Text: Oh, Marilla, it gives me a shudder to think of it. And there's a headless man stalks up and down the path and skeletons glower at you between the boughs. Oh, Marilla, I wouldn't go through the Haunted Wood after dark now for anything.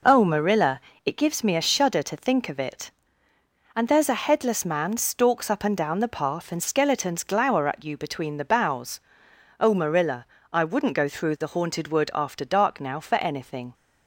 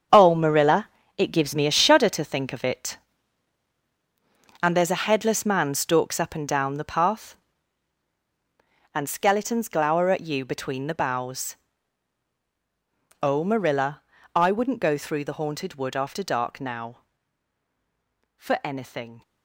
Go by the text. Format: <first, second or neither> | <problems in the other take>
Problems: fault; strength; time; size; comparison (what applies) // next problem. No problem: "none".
first | gets quieter; strong; throughout; 10.5 dB